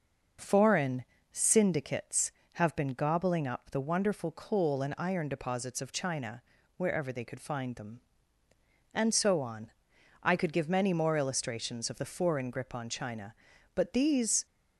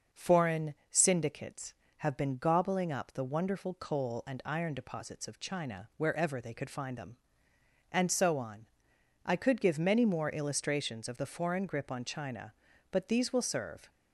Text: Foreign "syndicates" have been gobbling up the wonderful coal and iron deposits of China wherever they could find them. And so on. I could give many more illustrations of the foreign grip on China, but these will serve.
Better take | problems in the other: second | pauses between "Foreign" and "syndicates"; slight; at 1.0 s; 0.28 s long; slight in the second // pauses between "China" and "wherever"; slight; at 6.4 s; 0.36 s long // stops before "will serve"; at 14.4 s

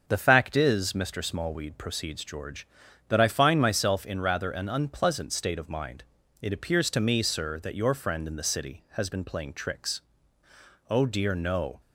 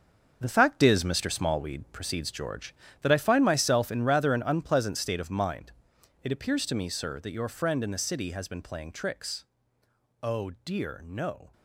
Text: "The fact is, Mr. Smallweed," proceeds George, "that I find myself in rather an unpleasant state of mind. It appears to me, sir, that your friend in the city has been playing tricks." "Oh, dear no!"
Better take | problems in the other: first | gets quieter; strong; throughout; 9.5 dB // starts louder than the rest; until 1.4 s; 7 dB; also in the first

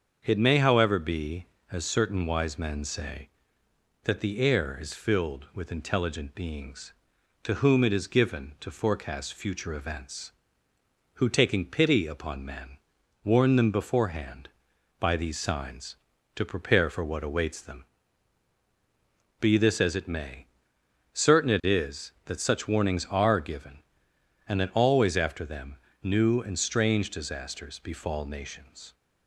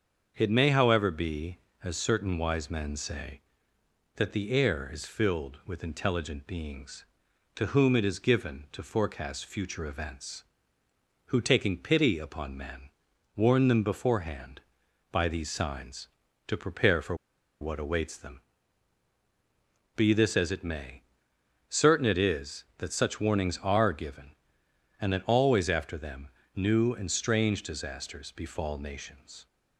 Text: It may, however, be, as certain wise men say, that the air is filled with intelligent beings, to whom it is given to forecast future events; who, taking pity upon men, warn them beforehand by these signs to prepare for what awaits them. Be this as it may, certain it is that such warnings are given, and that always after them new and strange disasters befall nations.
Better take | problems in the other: first | starts louder than the rest; until 1.3 s; 6.5 dB; also in the first // pauses between "for" and "what"; noticeable; at 17.1 s; 0.46 s long // pauses between "them" and "new"; slight; at 26.2 s; 0.26 s long; slight in the first

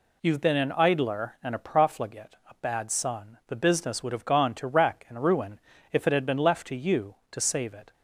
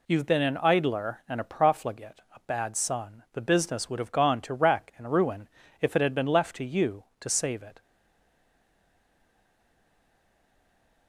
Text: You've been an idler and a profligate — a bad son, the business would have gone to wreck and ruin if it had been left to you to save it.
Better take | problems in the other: first | pauses between "ruin" and "if"; slight; at 5.4 s; 0.32 s long; slight in the first // stays silent after the last word; strong; from 7.8 s on; 3.2 s long

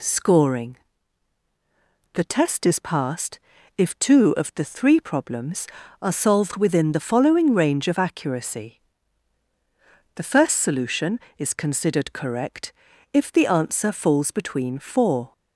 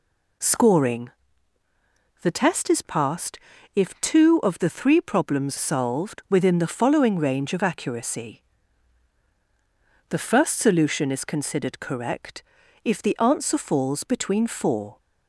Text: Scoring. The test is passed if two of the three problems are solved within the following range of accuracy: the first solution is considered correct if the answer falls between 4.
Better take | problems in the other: first | pauses between "passed" and "if"; slight; at 3.4 s; 0.34 s long; also in the first // skips "are"; at 5.5 s // pauses between "correct" and "if"; at 12.4 s; 0.40 s long; also in the first

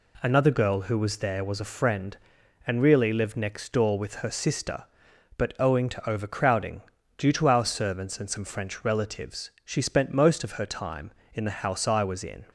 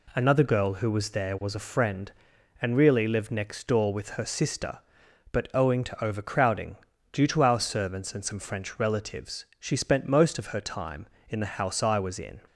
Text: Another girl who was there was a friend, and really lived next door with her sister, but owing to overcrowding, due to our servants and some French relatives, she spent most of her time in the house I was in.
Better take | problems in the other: neither | none

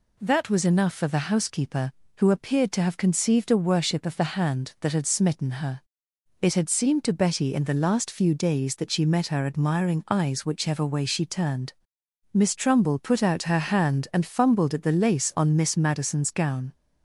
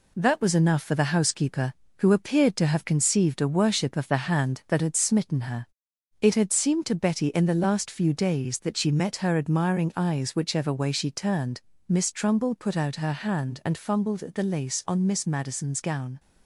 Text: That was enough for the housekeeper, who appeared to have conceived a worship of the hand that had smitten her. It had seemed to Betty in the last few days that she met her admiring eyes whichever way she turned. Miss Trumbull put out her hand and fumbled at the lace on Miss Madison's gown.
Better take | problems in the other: first | gets quieter; throughout; 3.5 dB

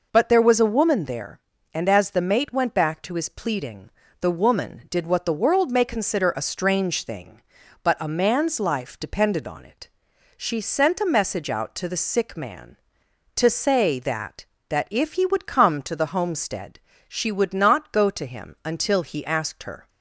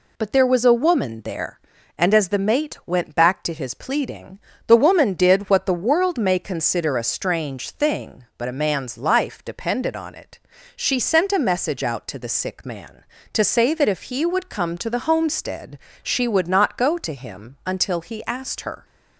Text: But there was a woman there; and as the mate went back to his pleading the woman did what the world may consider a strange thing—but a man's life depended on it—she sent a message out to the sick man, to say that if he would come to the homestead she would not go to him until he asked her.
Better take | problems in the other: second | pauses between "pleading" and "the"; slight; at 3.9 s; 0.30 s long; slight in the second // says "that" twice; at 14.7 s // pauses between "homestead" and "she"; slight; at 16.7 s; 0.28 s long; slight in the second

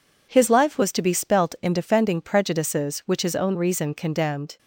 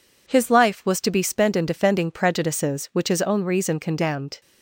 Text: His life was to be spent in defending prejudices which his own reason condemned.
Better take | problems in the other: second | says "spelt" for "spent"; at 1.1 s

